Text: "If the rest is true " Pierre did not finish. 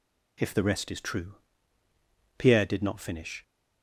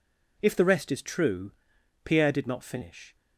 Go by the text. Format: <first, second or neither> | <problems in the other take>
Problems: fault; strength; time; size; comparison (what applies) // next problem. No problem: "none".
neither | none